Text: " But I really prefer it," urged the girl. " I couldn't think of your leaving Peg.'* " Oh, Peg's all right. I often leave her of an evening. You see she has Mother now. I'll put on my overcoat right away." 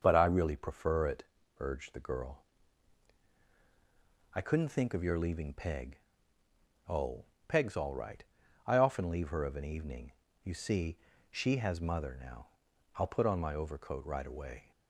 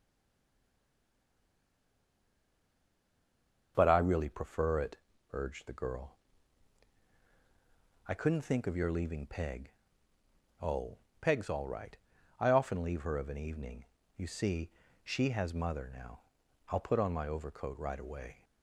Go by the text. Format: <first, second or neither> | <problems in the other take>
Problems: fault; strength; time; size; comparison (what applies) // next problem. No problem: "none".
first | stays silent before the first word; strong; until 3.7 s; 3.7 s long // starts louder than the rest; until 4.7 s; 6.5 dB; also in the first // pauses between "see" and "she"; slight; at 14.6 s; 0.34 s long; slight in the first